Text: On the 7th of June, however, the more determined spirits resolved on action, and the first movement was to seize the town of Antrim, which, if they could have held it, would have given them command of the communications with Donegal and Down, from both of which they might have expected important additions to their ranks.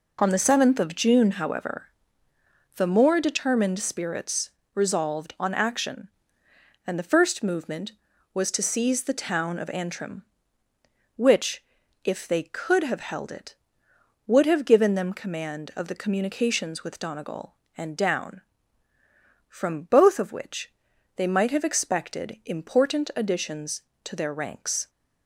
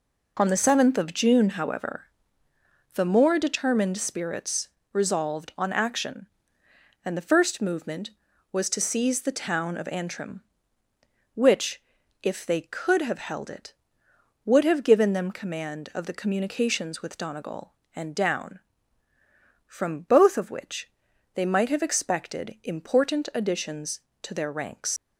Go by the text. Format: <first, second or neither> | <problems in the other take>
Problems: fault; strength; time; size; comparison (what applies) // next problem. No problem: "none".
first | pauses between "spirits" and "resolved"; slight; at 4.6 s; 0.24 s long; slight in the first // pauses between "which" and "they"; noticeable; at 20.8 s; 0.46 s long; noticeable in the first // leaves "ranks" unfinished; at 24.9 s; 115 ms